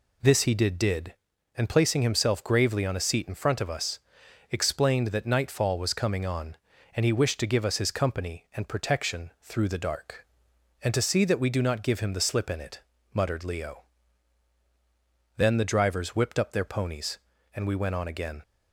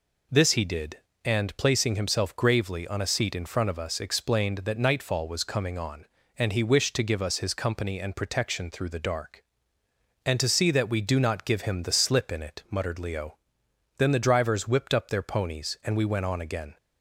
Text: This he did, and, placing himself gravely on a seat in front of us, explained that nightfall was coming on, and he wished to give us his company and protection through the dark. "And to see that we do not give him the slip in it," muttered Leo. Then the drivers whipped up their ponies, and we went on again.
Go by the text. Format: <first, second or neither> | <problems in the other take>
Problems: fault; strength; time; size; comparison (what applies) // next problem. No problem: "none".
second | says "did" twice; at 0.7 s